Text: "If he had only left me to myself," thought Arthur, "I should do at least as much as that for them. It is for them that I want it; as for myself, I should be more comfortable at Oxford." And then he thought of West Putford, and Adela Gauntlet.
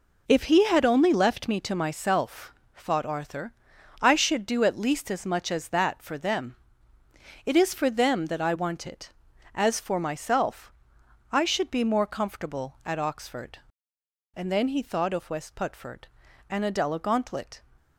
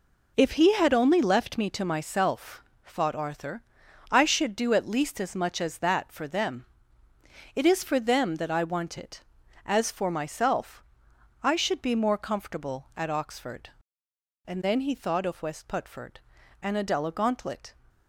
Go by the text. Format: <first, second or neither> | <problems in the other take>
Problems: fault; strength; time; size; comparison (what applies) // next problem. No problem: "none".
neither | none